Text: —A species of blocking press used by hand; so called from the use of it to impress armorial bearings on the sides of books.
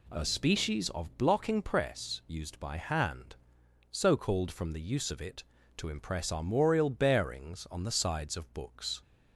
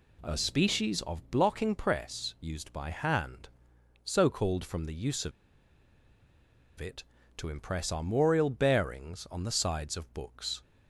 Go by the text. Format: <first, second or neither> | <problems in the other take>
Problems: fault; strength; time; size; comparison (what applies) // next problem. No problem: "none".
first | pauses between "of" and "it"; strong; at 5.3 s; 1.4 s long